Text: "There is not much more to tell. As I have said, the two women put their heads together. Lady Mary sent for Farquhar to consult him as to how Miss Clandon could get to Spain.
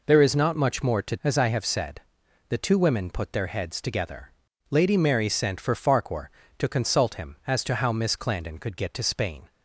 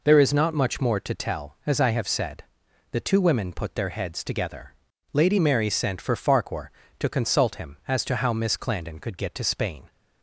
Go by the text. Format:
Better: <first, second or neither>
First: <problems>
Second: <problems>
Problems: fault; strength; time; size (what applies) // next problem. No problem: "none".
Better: second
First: skips "tell"; at 1.1 s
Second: none